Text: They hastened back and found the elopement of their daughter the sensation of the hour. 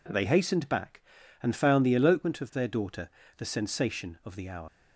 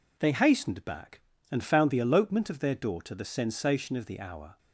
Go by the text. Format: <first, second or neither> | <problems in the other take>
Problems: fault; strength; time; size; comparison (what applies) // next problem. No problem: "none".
second | pauses between "daughter" and "the"; slight; at 3.0 s; 0.28 s long // leaves "hour" unfinished; at 4.6 s; 105 ms